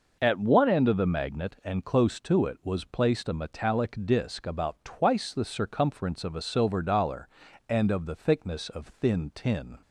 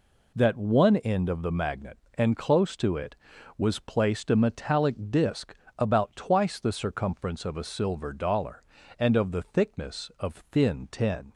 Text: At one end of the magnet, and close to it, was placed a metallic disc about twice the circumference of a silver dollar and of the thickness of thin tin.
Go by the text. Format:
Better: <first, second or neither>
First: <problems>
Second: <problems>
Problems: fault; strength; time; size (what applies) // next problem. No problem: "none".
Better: first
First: none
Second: says "That" for "At"; at 0.3 s // pauses between "disc" and "about"; slight; at 5.5 s; 0.22 s long